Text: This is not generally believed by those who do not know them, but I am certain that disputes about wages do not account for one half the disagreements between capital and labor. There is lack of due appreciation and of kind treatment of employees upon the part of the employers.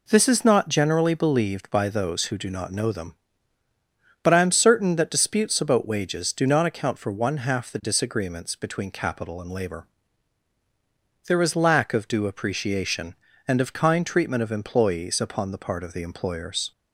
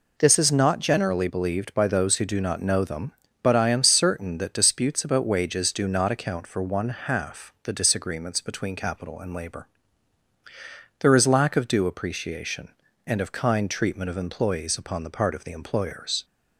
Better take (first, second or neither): neither